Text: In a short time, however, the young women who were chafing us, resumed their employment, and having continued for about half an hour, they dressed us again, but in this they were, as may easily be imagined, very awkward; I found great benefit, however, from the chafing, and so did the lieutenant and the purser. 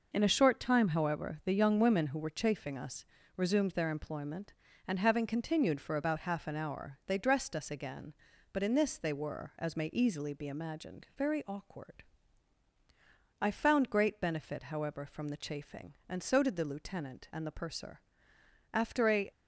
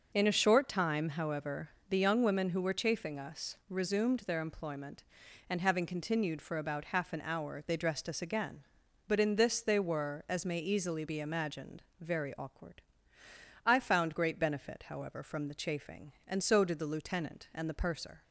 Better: second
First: goes on to say "After a"; from 18.7 s on; 0.56 s long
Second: none

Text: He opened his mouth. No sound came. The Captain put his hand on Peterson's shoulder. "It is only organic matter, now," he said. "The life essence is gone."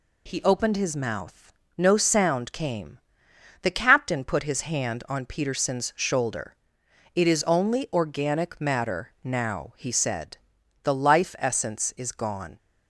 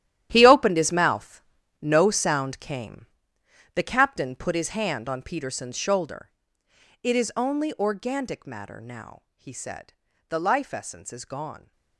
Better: first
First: none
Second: gets quieter; strong; throughout; 14.5 dB

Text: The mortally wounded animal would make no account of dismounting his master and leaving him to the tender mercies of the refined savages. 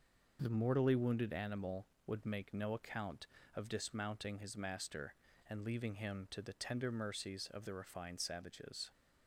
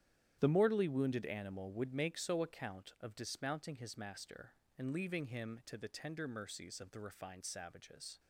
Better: first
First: none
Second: starts louder than the rest; strong; until 1.4 s; 11 dB // says "so" for "no"; at 2.1 s

